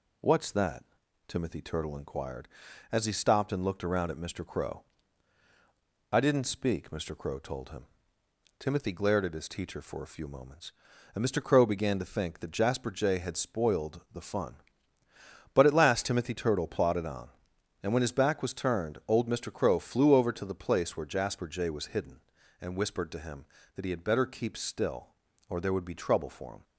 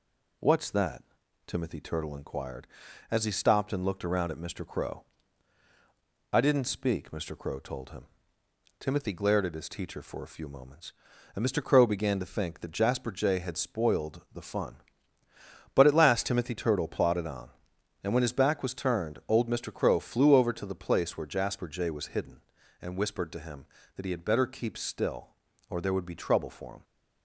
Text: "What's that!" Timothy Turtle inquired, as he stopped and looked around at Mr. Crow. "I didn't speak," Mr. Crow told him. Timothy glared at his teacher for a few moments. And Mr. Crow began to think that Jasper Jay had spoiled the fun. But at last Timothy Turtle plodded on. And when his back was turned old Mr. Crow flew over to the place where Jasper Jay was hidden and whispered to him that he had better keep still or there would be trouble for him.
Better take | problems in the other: neither | none

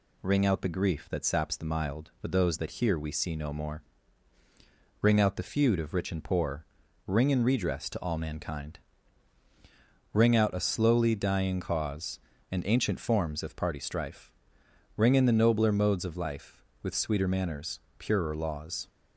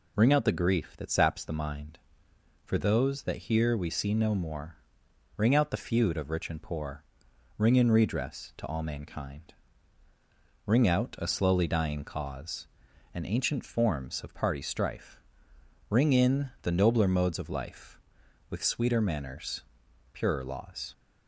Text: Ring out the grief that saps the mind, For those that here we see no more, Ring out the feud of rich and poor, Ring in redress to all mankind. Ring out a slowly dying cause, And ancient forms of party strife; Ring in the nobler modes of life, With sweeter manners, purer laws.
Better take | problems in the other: second | says "mild" for "mind"; at 1.6 s

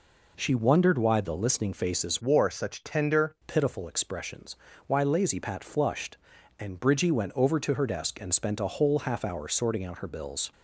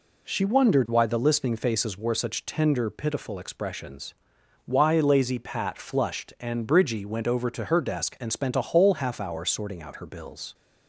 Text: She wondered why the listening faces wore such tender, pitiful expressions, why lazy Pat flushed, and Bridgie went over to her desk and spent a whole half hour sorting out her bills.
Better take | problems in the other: second | changes voice from "wore" to "tender"; from 2.2 to 3.3 s; 1.1 s long

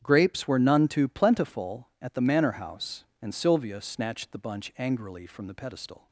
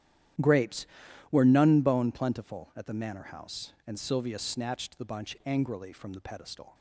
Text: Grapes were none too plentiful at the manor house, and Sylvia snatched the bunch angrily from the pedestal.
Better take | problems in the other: first | starts louder than the rest; strong; until 1.8 s; 11 dB; strong in the first // says "bone" for "too"; at 1.8 s

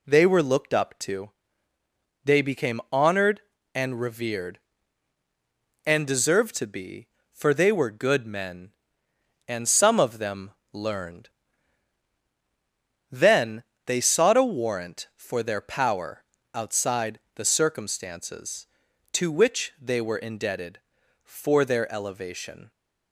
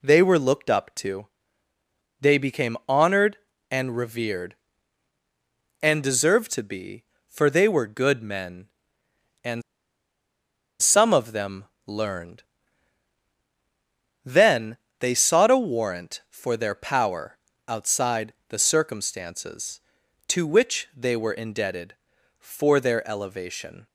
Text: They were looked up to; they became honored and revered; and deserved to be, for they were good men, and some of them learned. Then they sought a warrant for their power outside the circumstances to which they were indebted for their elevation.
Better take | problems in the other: first | pauses between "and" and "some"; at 9.6 s; 1.2 s long // pauses between "them" and "learned"; slight; at 11.6 s; 0.22 s long; slight in the first // pauses between "Then" and "they"; slight; at 14.7 s; 0.22 s long; slight in the first // pauses between "power" and "outside"; slight; at 17.3 s; 0.28 s long; slight in the first // pauses between "outside" and "the"; slight; at 18.3 s; 0.16 s long; slight in the first

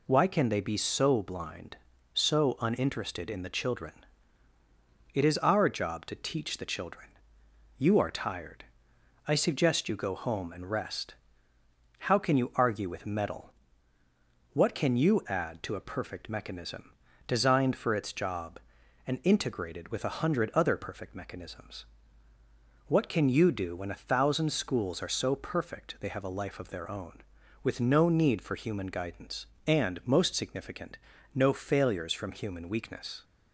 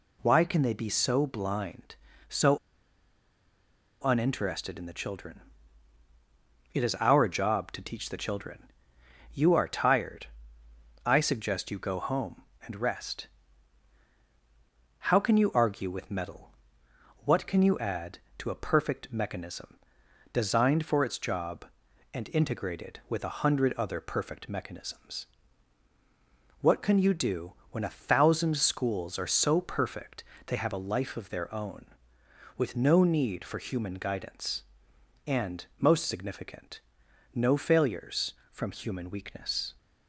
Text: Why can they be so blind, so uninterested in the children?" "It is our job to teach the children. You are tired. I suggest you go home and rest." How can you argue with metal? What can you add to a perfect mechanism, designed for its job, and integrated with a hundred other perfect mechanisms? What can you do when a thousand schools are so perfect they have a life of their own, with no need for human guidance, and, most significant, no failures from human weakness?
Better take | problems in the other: first | pauses between "so" and "uninterested"; strong; at 2.5 s; 1.4 s long // pauses between "do" and "when"; slight; at 27.5 s; 0.18 s long // pauses between "perfect" and "they"; slight; at 30.2 s; 0.24 s long

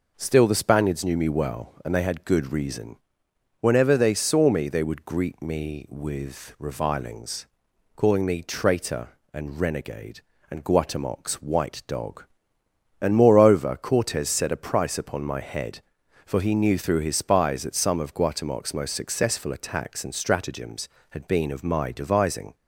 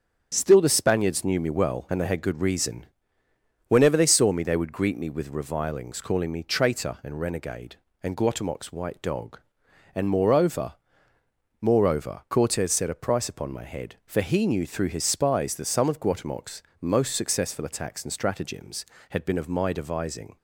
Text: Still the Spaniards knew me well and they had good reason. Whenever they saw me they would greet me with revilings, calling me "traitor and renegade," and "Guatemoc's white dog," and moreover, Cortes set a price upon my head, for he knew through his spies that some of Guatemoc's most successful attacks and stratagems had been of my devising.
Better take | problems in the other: first | starts louder than the rest; strong; until 1.3 s; 8 dB // says "moreover" twice; at 11.6 s // pauses between "Guatemoc's" and "most"; slight; at 16.6 s; 0.18 s long

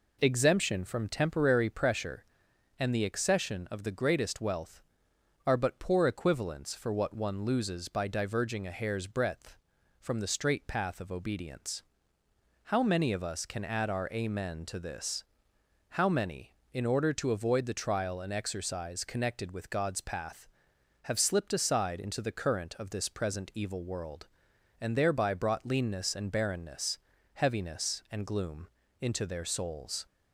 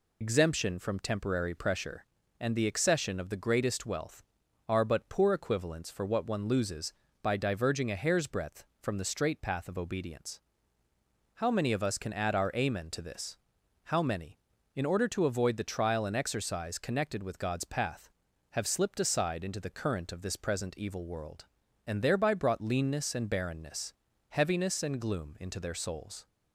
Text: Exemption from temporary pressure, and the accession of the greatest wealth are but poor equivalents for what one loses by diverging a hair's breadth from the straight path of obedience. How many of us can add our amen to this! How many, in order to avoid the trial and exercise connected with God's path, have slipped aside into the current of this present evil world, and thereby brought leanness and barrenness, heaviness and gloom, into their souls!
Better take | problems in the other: first | loses the start of "Exemption"; at 0.2 s; 55 ms

